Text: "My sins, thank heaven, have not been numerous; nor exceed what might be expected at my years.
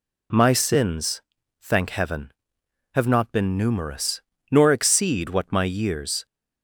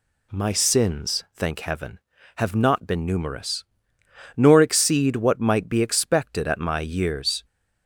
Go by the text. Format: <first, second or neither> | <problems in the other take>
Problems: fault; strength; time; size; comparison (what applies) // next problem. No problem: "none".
second | skips "might be expected at"; at 5.5 s